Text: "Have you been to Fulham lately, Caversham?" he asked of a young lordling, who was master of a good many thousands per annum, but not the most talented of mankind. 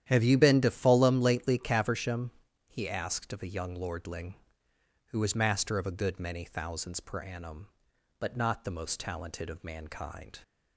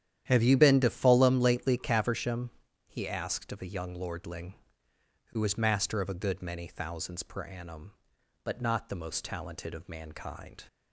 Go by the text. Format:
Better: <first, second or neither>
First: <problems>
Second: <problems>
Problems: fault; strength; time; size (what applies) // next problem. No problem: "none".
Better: neither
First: starts louder than the rest; strong; until 1.1 s; 10.5 dB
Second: starts louder than the rest; strong; until 1.2 s; 10.5 dB